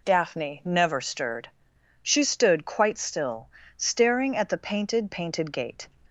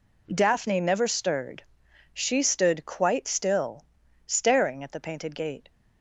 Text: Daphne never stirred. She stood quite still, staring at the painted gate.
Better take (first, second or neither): second